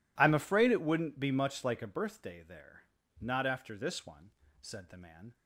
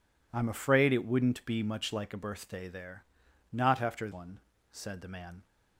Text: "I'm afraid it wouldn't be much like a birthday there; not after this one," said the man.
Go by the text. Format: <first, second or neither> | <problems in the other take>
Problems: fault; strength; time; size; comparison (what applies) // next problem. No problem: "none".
first | skips "this"; at 4.1 s